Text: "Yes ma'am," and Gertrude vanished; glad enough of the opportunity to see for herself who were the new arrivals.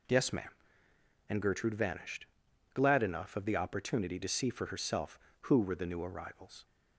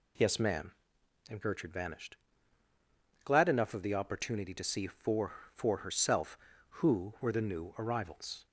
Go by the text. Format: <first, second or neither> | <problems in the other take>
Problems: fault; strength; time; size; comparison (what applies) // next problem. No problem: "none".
first | says "for" twice; at 5.5 s